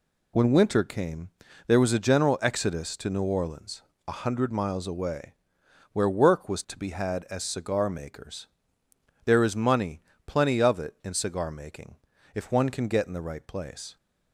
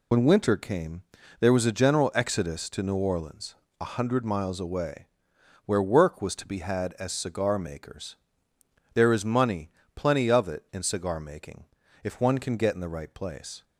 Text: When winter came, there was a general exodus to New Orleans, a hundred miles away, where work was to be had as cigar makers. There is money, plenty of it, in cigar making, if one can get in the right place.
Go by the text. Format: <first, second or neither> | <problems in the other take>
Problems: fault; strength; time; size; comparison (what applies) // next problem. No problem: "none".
first | loses the start of "When"; at 0.1 s; 40 ms